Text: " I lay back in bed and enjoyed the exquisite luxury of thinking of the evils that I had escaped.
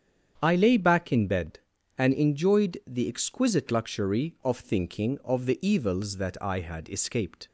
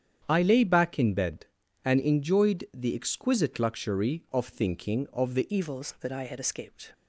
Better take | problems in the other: first | starts louder than the rest; strong; until 1.2 s; 8.5 dB; strong in the first // changes voice at "evils"; from 5.5 s on; 1.4 s long

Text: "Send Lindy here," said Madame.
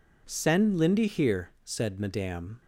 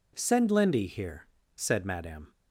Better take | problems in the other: neither | none

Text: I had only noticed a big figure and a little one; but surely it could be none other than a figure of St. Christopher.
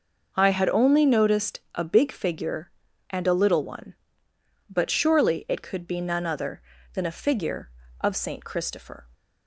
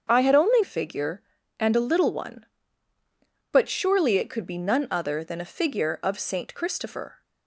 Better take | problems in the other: first | starts louder than the rest; until 1.1 s; 7 dB // skips "noticed a big"; at 0.6 s

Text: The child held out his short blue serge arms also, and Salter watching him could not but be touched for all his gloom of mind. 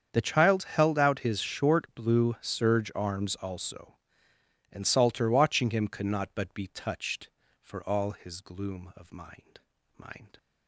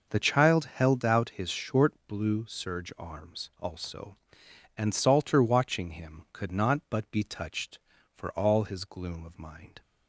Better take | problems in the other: second | starts louder than the rest; strong; until 1.1 s; 7.5 dB // says "mind" twice; at 9.9 s

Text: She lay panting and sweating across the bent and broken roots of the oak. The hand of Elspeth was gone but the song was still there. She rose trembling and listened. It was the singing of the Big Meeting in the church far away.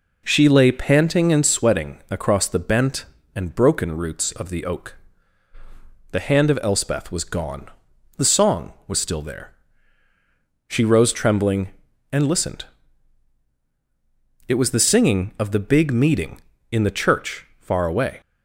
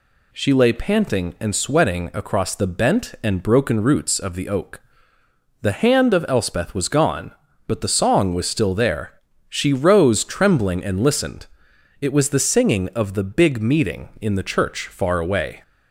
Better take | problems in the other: second | skips "but"; at 7.9 s

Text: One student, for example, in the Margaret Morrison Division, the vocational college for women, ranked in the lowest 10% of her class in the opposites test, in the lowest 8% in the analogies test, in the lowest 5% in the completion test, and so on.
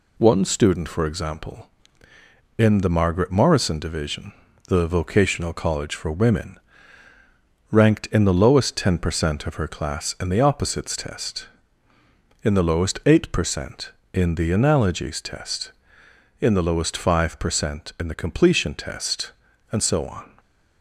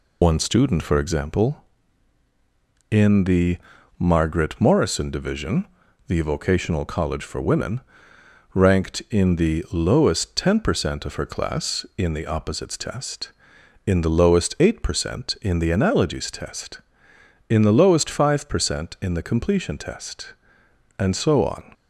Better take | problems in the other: first | loses the start of "One"; at 0.2 s; 55 ms // pauses between "the" and "Margaret"; at 3.5 s; 0.42 s long

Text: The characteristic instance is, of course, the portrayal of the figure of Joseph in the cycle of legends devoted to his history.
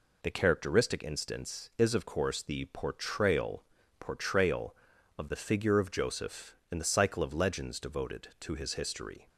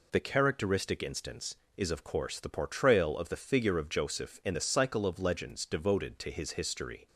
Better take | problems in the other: second | says "portrayal" twice; at 3.9 s

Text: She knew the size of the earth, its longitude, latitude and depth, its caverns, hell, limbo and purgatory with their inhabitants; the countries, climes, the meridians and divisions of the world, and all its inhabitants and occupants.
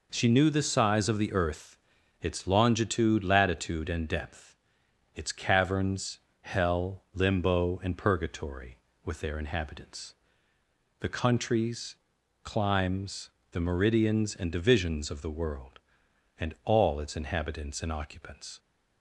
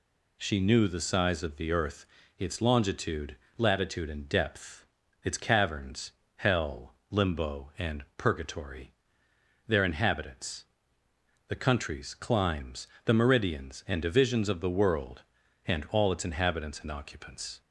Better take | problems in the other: first | skips "with"; at 9.2 s

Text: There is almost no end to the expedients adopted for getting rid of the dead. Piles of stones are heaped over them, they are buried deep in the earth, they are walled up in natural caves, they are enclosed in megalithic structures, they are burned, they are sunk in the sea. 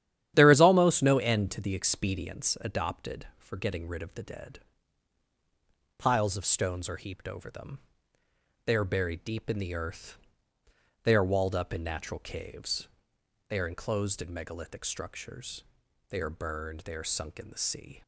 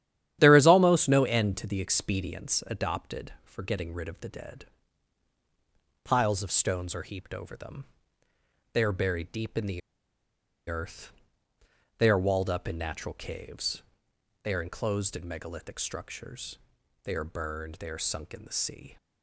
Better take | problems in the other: first | starts louder than the rest; strong; until 1.4 s; 11 dB; strong in the first // pauses between "the" and "earth"; noticeable; at 9.8 s; 0.88 s long

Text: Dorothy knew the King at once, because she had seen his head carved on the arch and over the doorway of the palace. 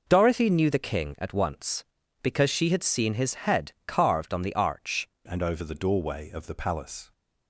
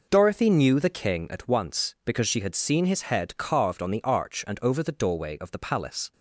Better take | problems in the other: second | changes voice at "and"; from 5.2 s on; 1.9 s long

